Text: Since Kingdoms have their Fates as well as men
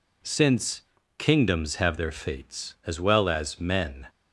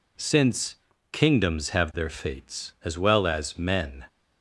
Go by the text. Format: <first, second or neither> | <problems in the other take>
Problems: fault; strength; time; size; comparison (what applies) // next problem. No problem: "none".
neither | pauses between "Since" and "Kingdoms"; slight; the same in both